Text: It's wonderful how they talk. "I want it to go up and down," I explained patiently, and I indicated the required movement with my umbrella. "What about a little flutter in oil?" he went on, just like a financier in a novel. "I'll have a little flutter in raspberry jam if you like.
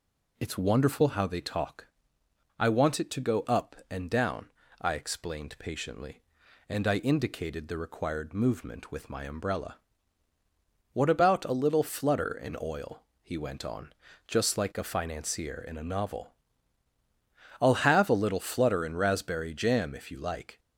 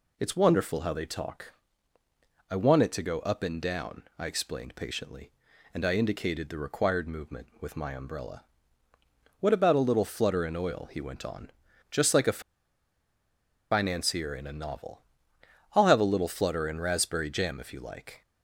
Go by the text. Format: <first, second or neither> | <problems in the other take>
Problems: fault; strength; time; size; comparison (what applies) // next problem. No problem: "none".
first | pauses between "a" and "financier"; strong; at 12.4 s; 1.3 s long